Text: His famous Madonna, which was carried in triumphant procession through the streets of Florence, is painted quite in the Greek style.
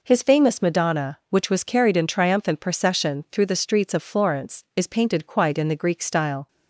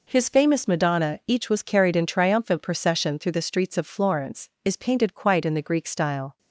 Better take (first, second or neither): first